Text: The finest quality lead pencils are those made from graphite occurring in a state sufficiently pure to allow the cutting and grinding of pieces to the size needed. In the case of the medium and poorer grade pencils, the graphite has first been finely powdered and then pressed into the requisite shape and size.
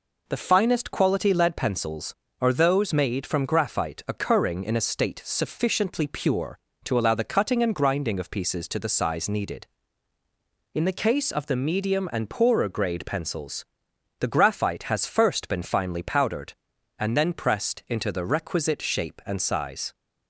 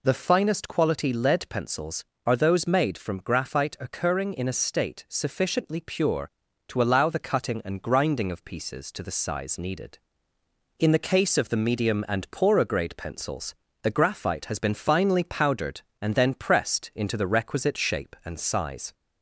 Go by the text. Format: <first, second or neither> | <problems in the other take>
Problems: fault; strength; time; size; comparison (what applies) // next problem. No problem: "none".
first | skips "first"; at 14.5 s